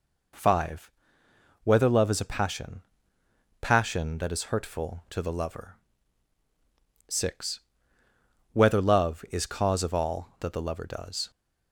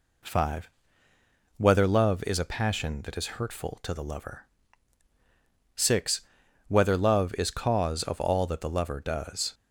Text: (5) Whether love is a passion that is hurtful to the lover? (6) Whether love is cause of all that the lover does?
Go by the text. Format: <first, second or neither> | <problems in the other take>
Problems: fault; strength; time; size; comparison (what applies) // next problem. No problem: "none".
second | says "passion" twice; at 3.6 s